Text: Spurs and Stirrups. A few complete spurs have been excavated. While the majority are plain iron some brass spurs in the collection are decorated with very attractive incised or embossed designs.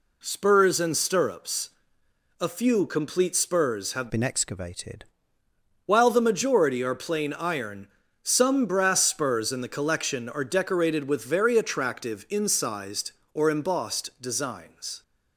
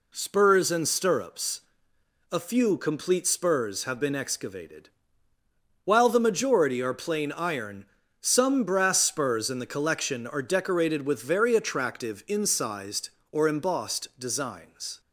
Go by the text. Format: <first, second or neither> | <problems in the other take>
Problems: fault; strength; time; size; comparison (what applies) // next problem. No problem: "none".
second | changes voice from "been" to "excavated"; from 4.1 to 5.0 s; 0.9 s long // pauses between "iron" and "some"; slight; at 7.8 s; 0.34 s long; slight in the second